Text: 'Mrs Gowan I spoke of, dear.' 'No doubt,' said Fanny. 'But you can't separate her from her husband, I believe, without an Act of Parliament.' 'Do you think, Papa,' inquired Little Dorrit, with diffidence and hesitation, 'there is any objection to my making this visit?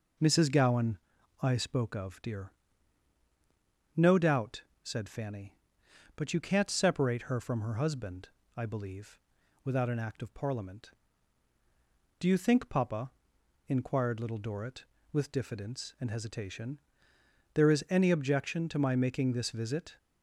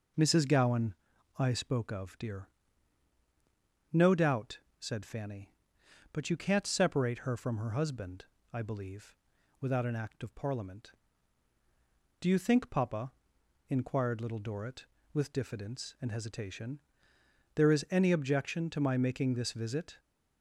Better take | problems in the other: neither | pauses between "Gowan" and "I"; the same in both

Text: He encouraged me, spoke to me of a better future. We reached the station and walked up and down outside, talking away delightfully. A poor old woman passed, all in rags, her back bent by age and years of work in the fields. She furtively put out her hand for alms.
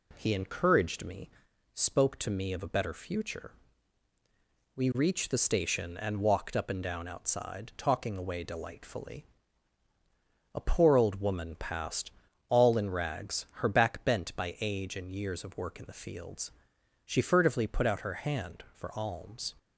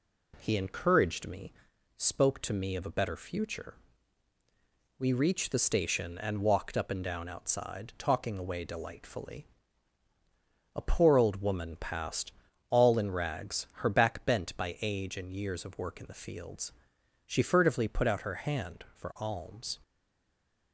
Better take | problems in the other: first | stays silent after the last word; slight; from 19.8 s on; 0.9 s long

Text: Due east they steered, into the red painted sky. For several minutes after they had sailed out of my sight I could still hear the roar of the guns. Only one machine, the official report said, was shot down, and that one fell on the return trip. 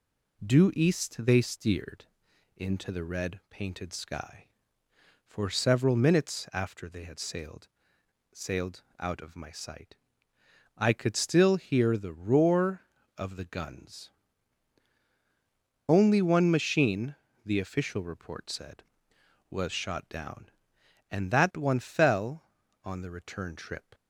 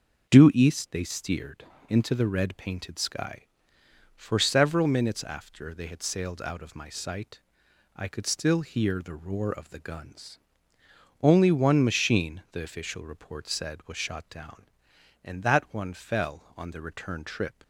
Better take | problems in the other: second | says "sailed" twice; at 8.3 s // pauses between "sight" and "I"; noticeable; at 9.9 s; 0.80 s long; noticeable in the second

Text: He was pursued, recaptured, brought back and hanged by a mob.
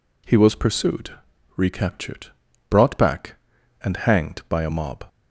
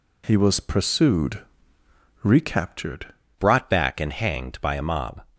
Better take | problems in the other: first | changes voice at "brought"; from 3.3 s on; 1.9 s long

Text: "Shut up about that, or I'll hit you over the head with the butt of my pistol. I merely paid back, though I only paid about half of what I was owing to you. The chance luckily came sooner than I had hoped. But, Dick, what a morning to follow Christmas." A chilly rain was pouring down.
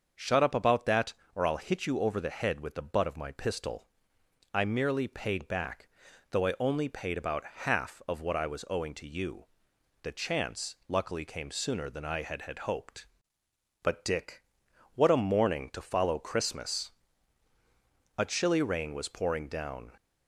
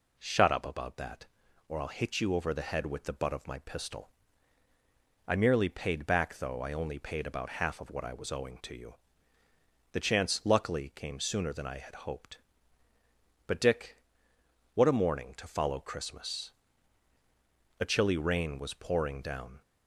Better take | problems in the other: second | starts louder than the rest; until 1.4 s; 6.5 dB // says "had" twice; at 12.4 s

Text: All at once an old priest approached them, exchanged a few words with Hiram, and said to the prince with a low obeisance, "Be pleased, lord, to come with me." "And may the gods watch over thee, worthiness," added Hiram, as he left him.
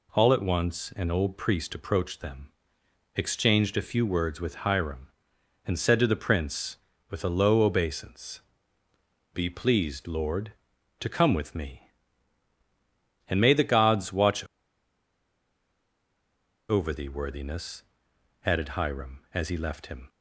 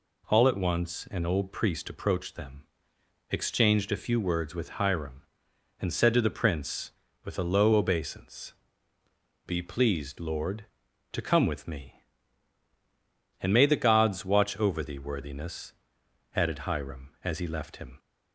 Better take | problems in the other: second | pauses between "watch" and "over"; strong; at 14.4 s; 2.2 s long

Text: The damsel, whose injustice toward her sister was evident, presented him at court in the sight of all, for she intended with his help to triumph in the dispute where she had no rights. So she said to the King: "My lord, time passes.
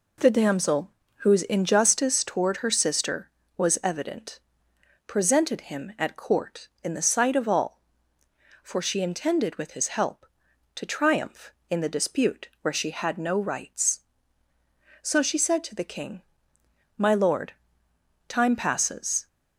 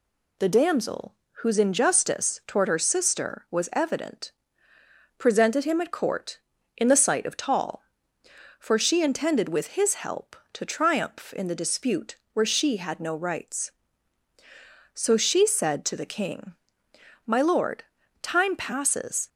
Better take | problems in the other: first | says "tall" for "all"; at 7.3 s // pauses between "dispute" and "where"; slight; at 12.1 s; 0.16 s long

